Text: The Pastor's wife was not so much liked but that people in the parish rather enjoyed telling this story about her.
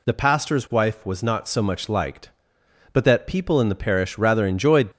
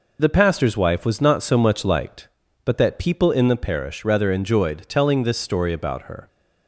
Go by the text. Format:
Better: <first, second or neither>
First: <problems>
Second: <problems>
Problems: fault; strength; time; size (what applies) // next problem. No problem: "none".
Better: second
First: stops before "telling this story about her"; at 4.9 s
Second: none